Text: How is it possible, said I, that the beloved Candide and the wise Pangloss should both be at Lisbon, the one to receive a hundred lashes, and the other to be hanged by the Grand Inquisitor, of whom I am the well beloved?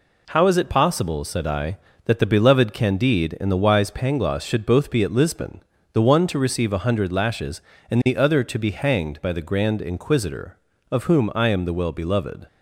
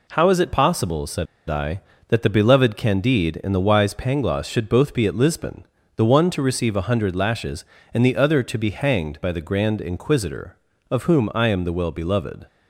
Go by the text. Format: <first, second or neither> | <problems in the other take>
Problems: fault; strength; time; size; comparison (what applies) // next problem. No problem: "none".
first | pauses between "said" and "I"; slight; at 1.2 s; 0.23 s long